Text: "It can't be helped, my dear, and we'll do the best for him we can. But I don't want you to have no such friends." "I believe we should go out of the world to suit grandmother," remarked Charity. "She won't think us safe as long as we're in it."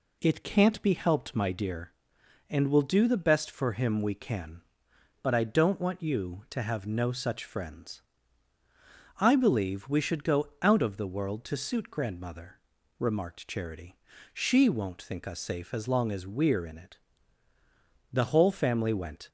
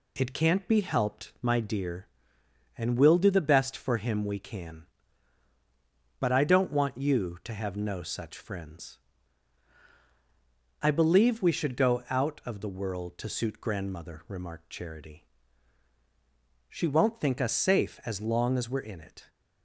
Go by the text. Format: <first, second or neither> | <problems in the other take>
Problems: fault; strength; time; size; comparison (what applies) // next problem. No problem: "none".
second | goes on to say "The whole family went"; noticeable; from 18.1 s on; 1.1 s long